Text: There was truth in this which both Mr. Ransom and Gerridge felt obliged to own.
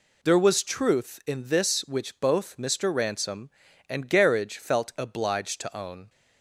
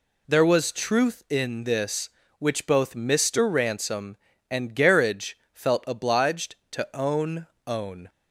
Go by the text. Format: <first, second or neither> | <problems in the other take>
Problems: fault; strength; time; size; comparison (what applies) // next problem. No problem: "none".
first | pauses between "Gerridge" and "felt"; slight; at 5.3 s; 0.18 s long // says "own" twice; at 7.6 s